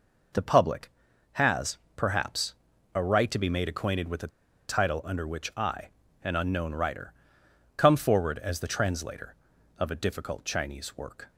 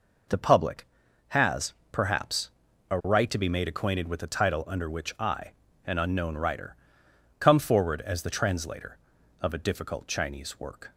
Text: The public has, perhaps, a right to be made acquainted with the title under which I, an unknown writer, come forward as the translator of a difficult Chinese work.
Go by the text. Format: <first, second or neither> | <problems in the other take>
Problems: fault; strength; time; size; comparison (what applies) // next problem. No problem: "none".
second | pauses between "the" and "title"; at 4.2 s; 0.39 s long